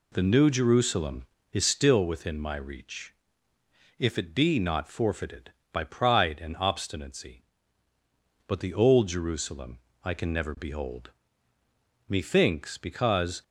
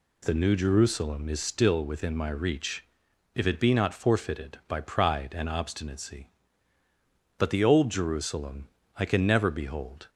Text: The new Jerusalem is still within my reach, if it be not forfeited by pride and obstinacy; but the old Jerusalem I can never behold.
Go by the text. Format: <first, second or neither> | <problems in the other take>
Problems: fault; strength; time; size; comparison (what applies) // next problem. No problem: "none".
second | pauses between "Jerusalem" and "I"; slight; at 9.7 s; 0.26 s long; slight in the second // goes on to say "Methinks because"; from 12.0 s on; 1.3 s long